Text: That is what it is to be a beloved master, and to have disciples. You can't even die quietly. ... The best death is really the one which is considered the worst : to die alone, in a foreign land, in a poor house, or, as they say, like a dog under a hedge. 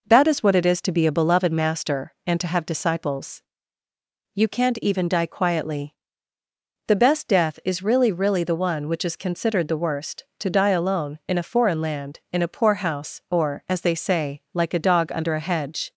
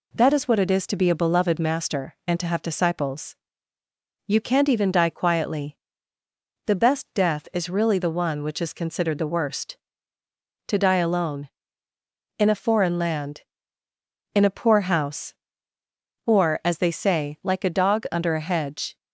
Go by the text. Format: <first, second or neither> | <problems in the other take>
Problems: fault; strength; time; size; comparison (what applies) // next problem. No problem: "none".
second | says "really" twice; at 8.1 s